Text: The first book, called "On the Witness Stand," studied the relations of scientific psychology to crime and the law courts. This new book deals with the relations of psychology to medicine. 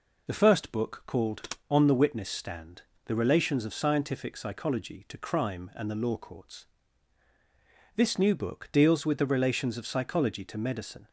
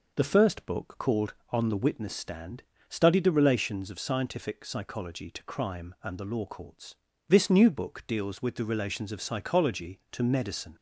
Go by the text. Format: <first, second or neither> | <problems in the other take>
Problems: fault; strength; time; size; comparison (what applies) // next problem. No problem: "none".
second | skips "studied"; at 2.9 s